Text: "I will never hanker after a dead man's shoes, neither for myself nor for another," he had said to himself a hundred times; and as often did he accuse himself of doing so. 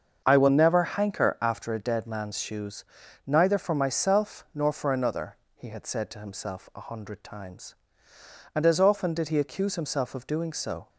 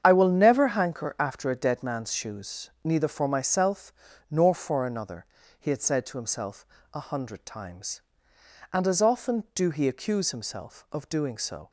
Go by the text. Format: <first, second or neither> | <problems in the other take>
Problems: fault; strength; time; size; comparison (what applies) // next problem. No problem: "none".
first | starts louder than the rest; strong; until 1.0 s; 8 dB; also in the first // pauses between "myself" and "nor"; at 3.9 s; 0.38 s long // pauses between "himself" and "a"; slight; at 6.6 s; 0.26 s long // says "do" for "did"; at 9.5 s